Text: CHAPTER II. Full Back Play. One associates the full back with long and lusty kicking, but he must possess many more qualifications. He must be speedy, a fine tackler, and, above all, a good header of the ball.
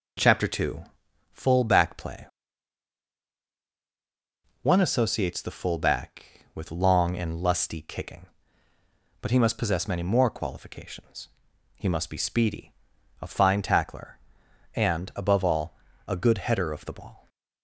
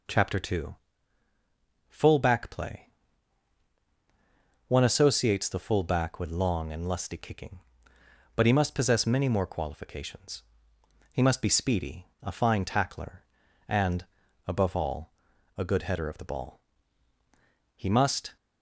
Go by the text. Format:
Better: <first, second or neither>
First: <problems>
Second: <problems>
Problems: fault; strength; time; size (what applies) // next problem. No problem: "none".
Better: first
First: none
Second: goes on to say "He must"; noticeable; from 17.7 s on; 0.62 s long